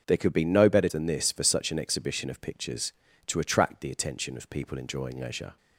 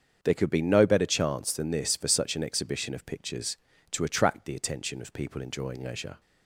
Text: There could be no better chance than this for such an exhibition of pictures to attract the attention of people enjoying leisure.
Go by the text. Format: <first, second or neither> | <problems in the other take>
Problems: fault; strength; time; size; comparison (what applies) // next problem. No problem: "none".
second | starts louder than the rest; until 1.0 s; 6.5 dB; also in the second // skips "chance"; at 0.8 s